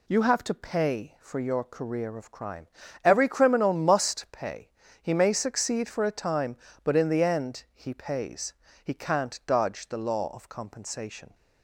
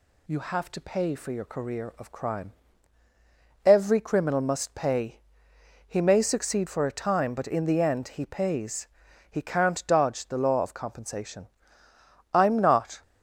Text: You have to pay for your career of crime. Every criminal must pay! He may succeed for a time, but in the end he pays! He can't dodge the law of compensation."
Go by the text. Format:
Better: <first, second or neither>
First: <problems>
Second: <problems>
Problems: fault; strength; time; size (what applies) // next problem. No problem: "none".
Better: first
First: none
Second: goes on to say "I'm not"; noticeable; from 12.3 s on; 0.68 s long